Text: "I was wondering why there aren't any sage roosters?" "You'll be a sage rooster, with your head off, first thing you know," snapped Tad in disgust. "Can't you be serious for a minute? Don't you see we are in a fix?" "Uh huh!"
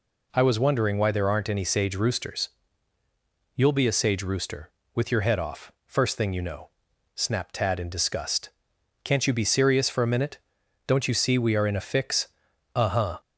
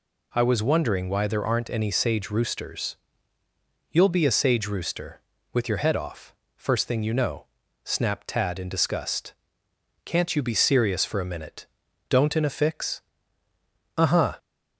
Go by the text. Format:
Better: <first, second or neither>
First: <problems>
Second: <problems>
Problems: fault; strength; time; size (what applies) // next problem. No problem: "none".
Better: first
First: none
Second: skips "you see we are"; at 12.3 s